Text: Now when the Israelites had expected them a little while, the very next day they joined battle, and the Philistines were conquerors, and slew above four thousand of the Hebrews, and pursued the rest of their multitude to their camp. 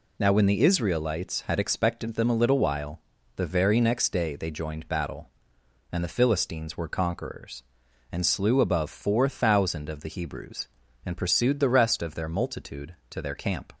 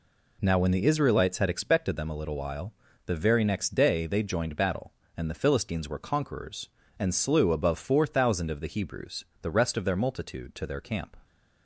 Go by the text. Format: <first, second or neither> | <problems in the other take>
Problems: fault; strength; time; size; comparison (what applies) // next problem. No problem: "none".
first | skips "and pursued"; at 9.3 s